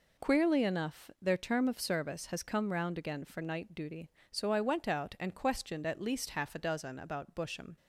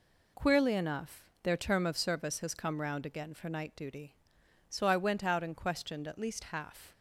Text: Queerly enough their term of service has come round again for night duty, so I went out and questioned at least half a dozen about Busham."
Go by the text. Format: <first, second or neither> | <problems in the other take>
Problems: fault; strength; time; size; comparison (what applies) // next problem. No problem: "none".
first | pauses between "enough" and "their"; slight; at 1.2 s; 0.18 s long // stops before "a dozen about Busham"; at 6.9 s